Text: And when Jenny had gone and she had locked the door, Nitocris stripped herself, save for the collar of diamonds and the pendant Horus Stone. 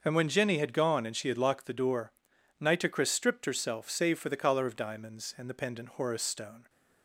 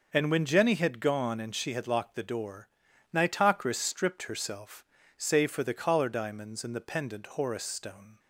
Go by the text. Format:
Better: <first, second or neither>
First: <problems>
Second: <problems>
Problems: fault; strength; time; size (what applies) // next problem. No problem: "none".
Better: first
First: none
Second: skips "of"; at 6.0 s